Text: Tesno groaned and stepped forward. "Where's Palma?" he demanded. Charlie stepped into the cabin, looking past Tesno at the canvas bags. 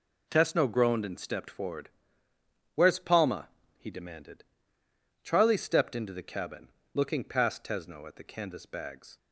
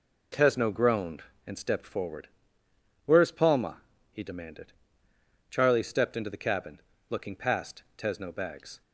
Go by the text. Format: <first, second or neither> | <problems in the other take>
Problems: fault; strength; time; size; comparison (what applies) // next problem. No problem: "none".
first | pauses between "past" and "Tesno"; slight; at 7.8 s; 0.16 s long // skips "at the canvas"; at 8.3 s